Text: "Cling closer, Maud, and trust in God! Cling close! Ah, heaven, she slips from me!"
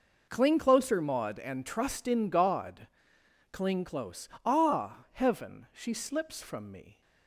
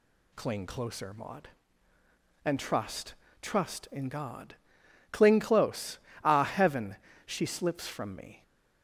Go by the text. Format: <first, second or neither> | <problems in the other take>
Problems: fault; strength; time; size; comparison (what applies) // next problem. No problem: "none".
first | says "trust" twice; at 3.4 s